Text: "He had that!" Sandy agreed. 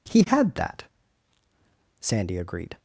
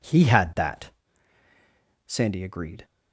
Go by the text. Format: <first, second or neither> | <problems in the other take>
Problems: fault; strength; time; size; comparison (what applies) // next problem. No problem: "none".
neither | none